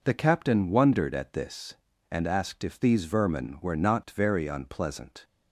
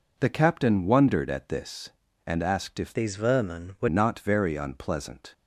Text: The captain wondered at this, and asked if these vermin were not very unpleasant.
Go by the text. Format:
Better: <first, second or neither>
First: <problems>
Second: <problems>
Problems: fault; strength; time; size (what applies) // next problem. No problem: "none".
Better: first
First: none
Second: changes voice from "these" to "were"; from 2.9 to 3.8 s; 0.9 s long